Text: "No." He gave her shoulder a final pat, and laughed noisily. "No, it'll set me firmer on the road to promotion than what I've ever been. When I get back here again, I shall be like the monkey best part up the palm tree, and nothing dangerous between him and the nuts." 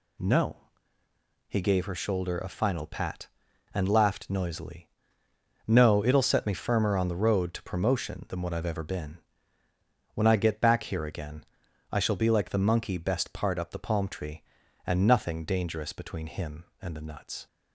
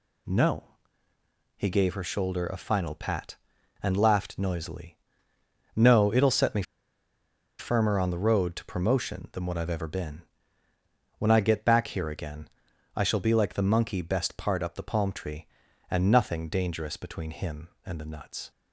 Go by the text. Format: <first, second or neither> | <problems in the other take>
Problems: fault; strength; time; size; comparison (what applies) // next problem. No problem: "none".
first | pauses between "me" and "firmer"; noticeable; at 6.6 s; 0.96 s long